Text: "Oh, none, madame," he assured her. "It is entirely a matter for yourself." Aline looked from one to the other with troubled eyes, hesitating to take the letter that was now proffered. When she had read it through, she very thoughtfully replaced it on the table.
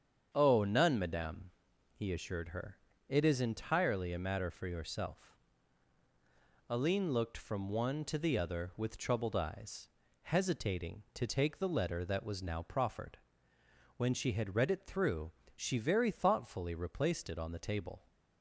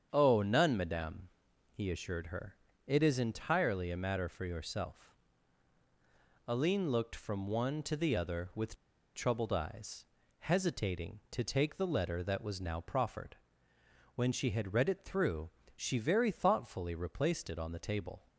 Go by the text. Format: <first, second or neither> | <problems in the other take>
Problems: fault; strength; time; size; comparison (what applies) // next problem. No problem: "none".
first | starts louder than the rest; strong; until 1.1 s; 7.5 dB; strong in the first // pauses between "with" and "troubled"; at 8.7 s; 0.41 s long